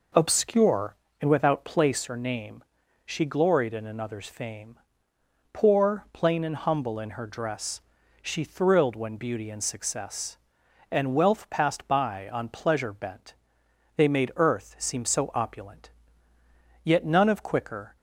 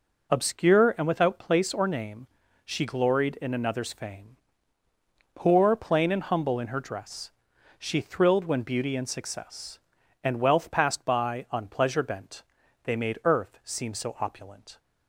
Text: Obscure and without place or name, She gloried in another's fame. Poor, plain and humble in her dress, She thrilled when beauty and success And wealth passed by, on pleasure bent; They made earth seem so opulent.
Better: second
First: goes on to say "Yet none of quicker"; noticeable; from 16.8 s on; 1.1 s long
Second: none

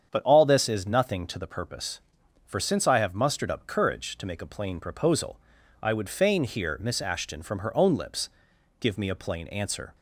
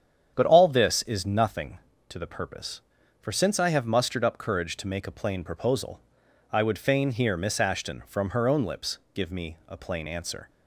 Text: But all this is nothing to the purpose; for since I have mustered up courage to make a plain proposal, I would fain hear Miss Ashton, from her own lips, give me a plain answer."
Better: neither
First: starts louder than the rest; strong; until 1.1 s; 8 dB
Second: starts louder than the rest; strong; until 1.3 s; 8.5 dB

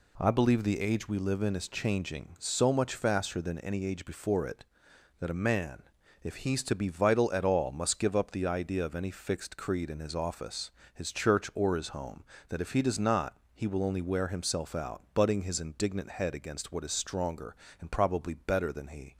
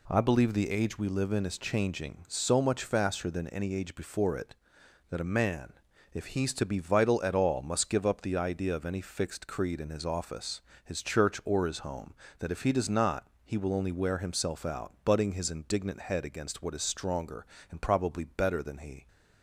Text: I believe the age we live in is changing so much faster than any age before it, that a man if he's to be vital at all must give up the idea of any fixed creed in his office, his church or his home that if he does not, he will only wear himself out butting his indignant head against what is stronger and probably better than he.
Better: neither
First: pauses between "man" and "if"; at 5.8 s; 0.40 s long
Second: pauses between "man" and "if"; at 5.7 s; 0.40 s long

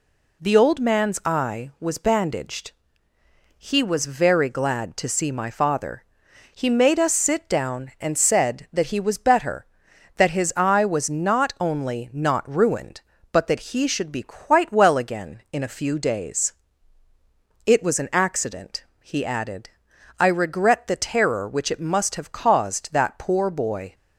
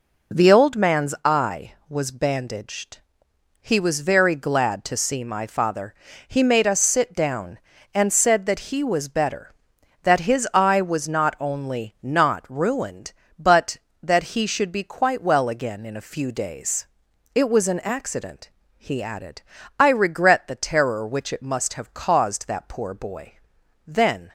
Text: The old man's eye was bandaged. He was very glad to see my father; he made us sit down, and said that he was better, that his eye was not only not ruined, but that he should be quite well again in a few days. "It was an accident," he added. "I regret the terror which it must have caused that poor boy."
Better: first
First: none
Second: goes on to say "Then"; slight; from 23.8 s on; 0.46 s long

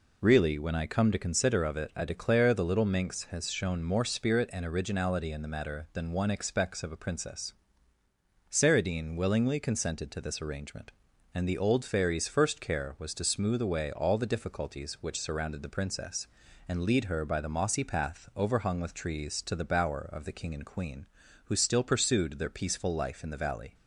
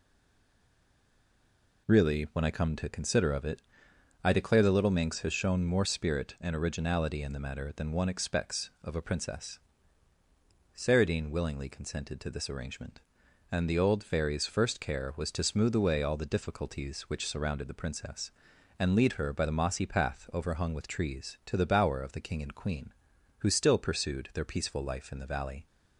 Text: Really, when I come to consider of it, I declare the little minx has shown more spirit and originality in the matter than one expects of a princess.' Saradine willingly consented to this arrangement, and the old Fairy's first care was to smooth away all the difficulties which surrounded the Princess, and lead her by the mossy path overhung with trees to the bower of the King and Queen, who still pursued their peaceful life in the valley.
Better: first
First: none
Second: stays silent before the first word; noticeable; until 1.8 s; 1.8 s long

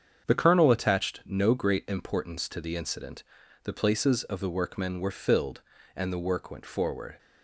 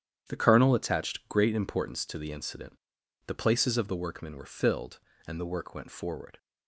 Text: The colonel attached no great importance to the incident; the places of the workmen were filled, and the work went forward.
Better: first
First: starts louder than the rest; strong; until 1.3 s; 7.5 dB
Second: starts louder than the rest; strong; until 1.3 s; 9.5 dB // skips "no"; at 1.2 s

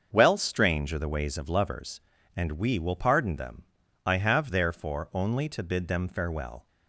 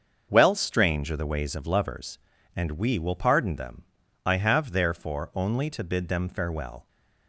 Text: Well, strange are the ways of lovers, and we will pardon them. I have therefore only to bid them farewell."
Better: neither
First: starts louder than the rest; until 1.1 s; 6.5 dB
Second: starts louder than the rest; until 1.3 s; 6.5 dB

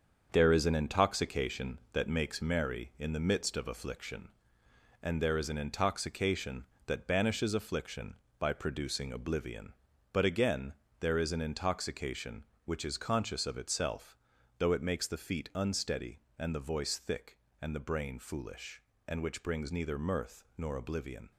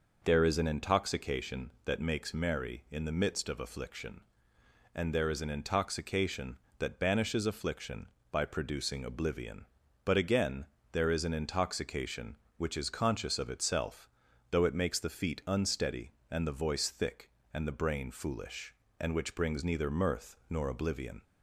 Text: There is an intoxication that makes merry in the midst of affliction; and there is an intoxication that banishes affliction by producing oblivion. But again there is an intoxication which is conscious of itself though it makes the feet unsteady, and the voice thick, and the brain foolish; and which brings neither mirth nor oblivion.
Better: second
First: gets quieter; throughout; 7 dB // pauses between "again" and "there"; slight; at 10.7 s; 0.26 s long // pauses between "itself" and "though"; at 14.1 s; 0.42 s long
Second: pauses between "again" and "there"; slight; at 10.6 s; 0.26 s long // pauses between "itself" and "though"; at 14.0 s; 0.42 s long

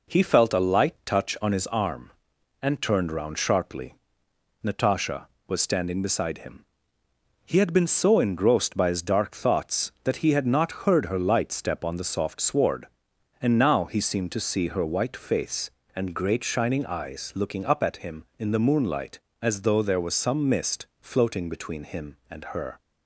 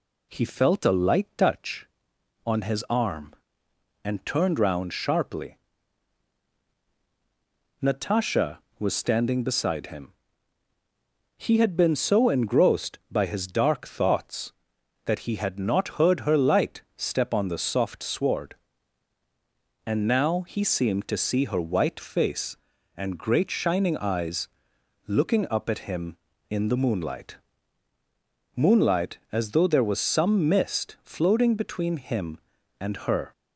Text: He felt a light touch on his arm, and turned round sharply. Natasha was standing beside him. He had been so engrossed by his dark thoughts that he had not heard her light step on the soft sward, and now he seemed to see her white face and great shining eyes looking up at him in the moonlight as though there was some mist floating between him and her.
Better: first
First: none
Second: pauses between "eyes" and "looking"; noticeable; at 24.4 s; 0.60 s long // says "moonlight" twice; at 28.5 s

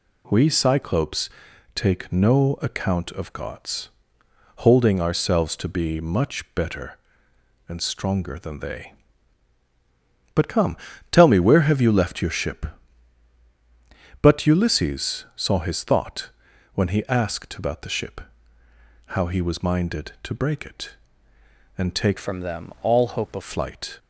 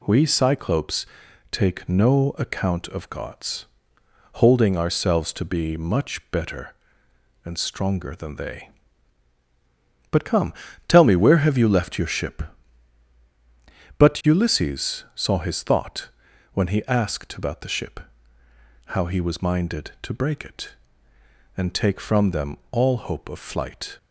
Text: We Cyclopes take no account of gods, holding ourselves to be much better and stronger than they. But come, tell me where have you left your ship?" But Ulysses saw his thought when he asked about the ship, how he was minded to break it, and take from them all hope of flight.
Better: second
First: pauses between "Cyclopes" and "take"; noticeable; at 1.2 s; 0.46 s long // pauses between "thought" and "when"; at 16.2 s; 0.44 s long // changes voice from "from" to "of"; from 22.1 to 23.4 s; 1.3 s long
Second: pauses between "Cyclopes" and "take"; noticeable; at 1.0 s; 0.46 s long // pauses between "thought" and "when"; at 16.0 s; 0.44 s long

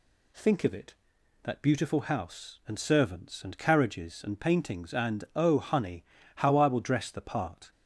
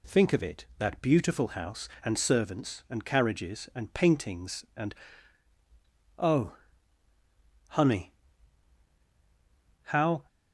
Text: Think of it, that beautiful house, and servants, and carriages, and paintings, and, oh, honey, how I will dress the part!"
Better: first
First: none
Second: stops before "I will dress the part"; at 10.2 s

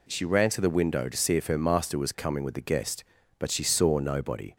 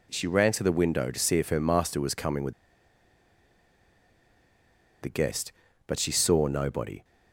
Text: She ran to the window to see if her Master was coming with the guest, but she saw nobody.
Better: first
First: none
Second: pauses between "with" and "the"; strong; at 2.5 s; 2.5 s long

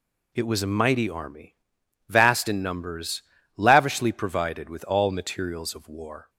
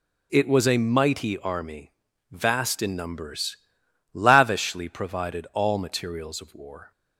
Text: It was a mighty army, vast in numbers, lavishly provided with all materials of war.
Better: first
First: none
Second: skips "with"; at 5.5 s

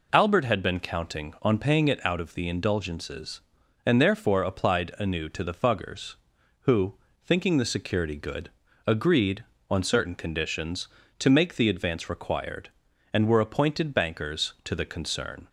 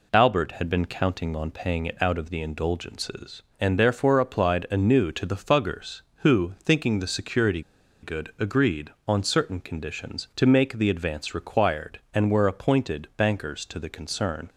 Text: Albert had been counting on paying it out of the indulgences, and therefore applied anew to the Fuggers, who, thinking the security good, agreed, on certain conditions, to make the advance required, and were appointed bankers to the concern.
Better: first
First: none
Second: pauses between "security" and "good"; at 7.6 s; 0.41 s long

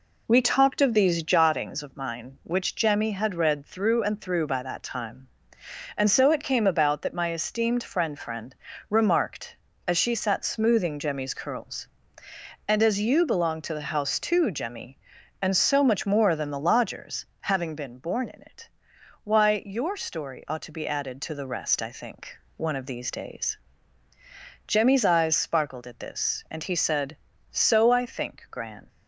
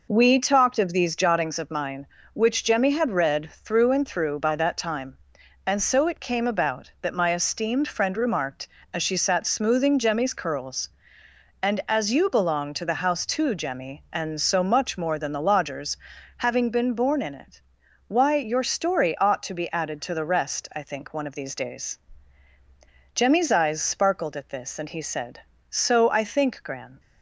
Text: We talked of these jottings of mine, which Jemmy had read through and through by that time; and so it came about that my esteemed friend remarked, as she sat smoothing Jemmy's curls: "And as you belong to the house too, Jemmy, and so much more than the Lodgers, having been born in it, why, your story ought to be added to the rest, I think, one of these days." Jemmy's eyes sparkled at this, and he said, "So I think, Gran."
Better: second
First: says "friend" twice; at 8.1 s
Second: none

